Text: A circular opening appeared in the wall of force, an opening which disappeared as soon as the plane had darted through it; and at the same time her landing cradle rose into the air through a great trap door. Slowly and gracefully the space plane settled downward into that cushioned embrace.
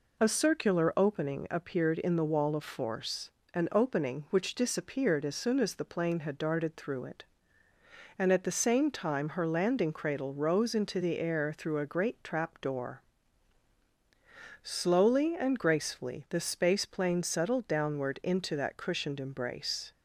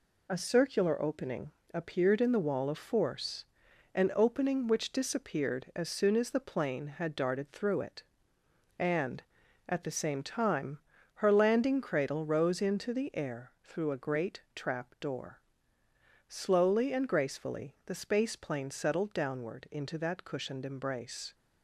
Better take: first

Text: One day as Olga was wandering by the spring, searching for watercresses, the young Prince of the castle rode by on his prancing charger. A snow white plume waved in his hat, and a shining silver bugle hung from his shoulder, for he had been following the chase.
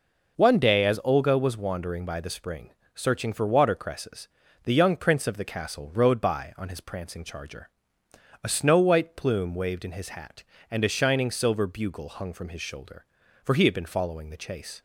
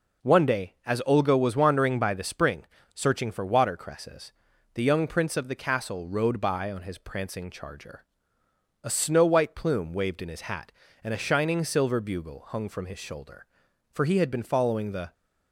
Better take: first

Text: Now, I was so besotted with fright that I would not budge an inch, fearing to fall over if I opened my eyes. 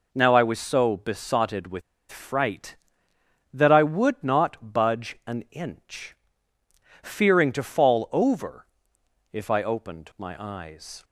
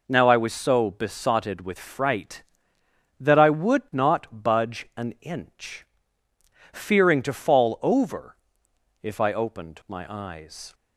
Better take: second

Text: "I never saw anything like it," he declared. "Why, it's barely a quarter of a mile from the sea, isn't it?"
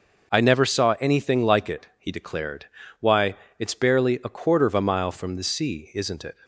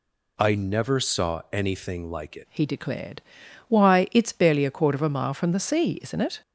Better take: first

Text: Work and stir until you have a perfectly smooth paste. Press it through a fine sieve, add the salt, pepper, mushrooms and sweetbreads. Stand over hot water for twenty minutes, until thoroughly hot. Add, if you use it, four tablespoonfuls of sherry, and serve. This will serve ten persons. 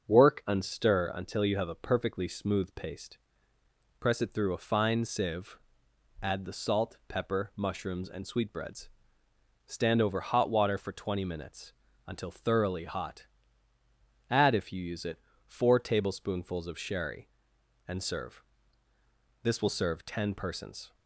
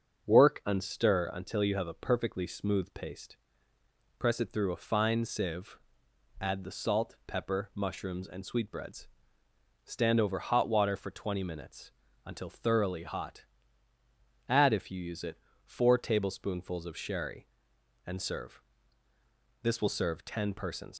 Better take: first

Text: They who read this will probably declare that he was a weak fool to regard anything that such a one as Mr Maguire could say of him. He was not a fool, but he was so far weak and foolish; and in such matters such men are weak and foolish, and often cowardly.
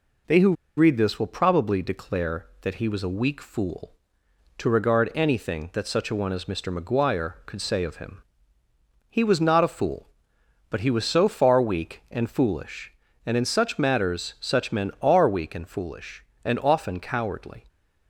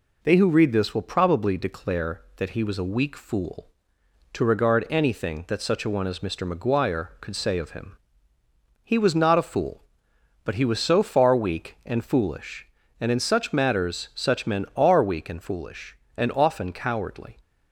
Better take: second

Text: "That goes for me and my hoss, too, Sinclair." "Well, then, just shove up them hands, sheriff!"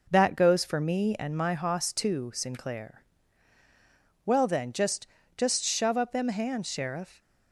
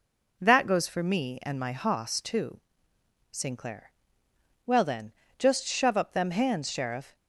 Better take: second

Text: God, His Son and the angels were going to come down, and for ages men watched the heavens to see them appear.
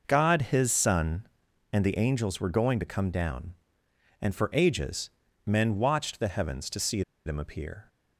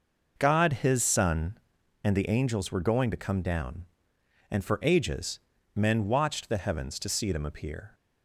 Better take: second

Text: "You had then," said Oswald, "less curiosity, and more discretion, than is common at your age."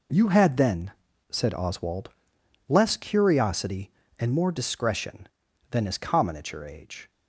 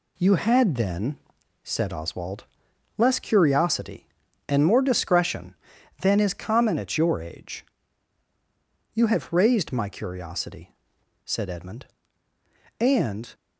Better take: first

